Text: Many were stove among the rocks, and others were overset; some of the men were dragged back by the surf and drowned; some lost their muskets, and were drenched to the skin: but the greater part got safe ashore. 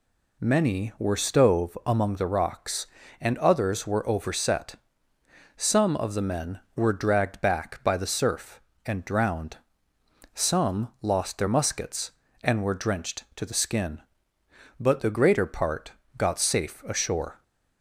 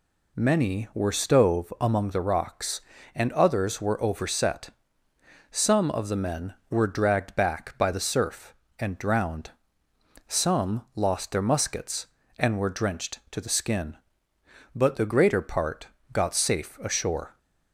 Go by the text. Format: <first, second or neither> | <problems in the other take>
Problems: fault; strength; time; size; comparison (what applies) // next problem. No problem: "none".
neither | pauses between "part" and "got"; slight; the same in both